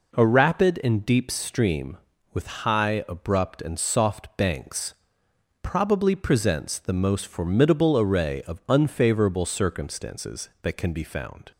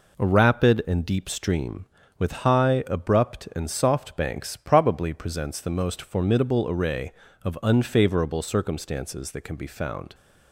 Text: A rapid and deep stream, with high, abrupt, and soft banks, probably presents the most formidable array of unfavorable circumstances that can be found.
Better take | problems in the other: neither | none

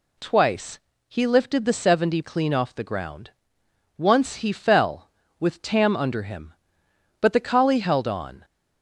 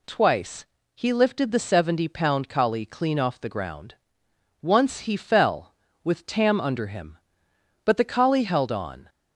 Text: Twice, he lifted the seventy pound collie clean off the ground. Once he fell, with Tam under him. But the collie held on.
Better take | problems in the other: second | skips "pound collie"; at 2.2 s

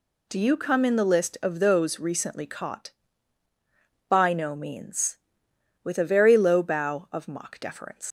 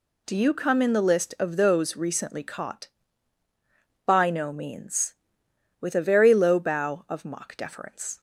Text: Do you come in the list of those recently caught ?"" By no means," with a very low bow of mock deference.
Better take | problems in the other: second | leaves "deference" unfinished; at 8.0 s; 125 ms

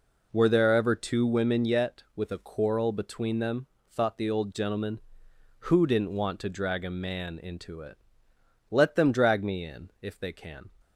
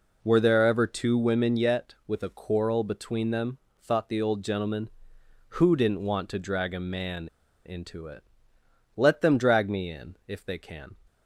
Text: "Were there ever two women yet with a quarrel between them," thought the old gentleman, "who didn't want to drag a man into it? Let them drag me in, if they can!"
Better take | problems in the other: first | pauses between "man" and "into"; at 7.2 s; 0.38 s long

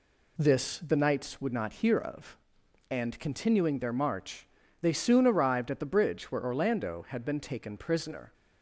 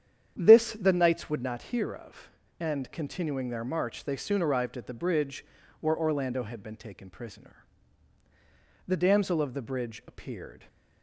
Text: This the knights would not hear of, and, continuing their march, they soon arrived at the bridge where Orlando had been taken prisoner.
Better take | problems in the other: first | starts louder than the rest; strong; until 1.3 s; 9 dB // pauses between "bridge" and "where"; at 5.4 s; 0.38 s long // goes on to say "The damsel of the bridge appeared"; strong; from 8.8 s on; 1.8 s long

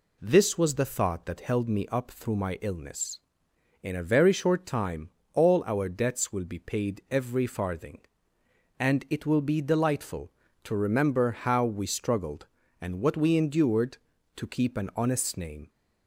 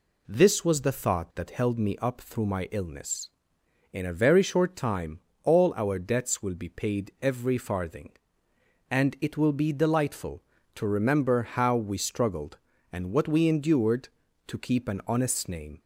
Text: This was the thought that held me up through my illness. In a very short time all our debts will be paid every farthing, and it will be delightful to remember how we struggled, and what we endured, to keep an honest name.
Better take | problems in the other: neither | pauses between "time" and "all"; slight; the same in both

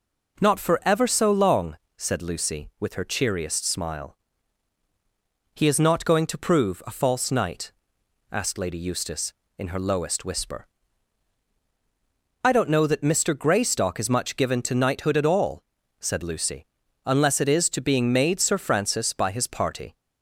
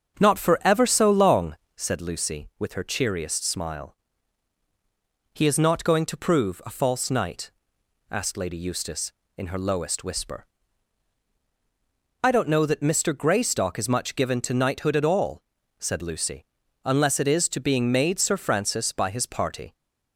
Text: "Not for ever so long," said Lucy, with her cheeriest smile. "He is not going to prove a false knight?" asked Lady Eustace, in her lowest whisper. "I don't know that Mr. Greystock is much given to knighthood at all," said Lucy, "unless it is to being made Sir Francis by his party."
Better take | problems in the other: first | starts louder than the rest; strong; until 1.9 s; 7.5 dB

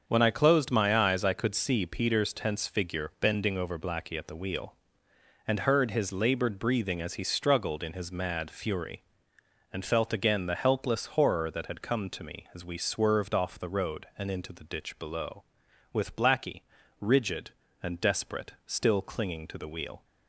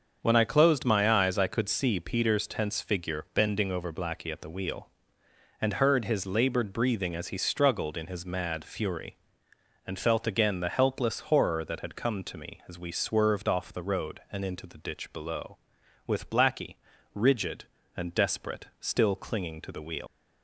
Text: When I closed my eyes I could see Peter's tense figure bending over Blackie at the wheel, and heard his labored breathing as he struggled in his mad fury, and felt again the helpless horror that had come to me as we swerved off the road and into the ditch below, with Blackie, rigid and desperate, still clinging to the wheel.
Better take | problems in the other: first | starts louder than the rest; until 1.2 s; 6.5 dB; also in the first // leaves "wheel" unfinished; at 20.0 s; 115 ms

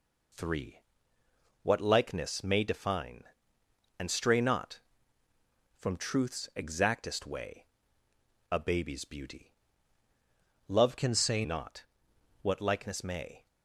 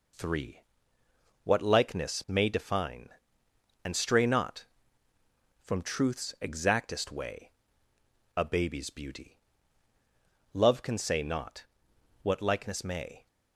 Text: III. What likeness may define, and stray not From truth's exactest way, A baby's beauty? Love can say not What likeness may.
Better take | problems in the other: second | changes voice from "can" to "say"; from 10.9 to 11.4 s; 0.5 s long // pauses between "not" and "What"; noticeable; at 11.8 s; 0.58 s long; noticeable in the second

